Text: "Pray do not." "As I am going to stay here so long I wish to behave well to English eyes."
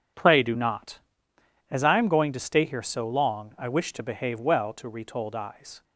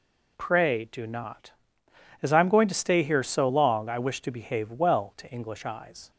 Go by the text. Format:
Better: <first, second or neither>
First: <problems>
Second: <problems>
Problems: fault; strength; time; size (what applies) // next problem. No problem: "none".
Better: second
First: says "Retold" for "English"; at 4.8 s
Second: none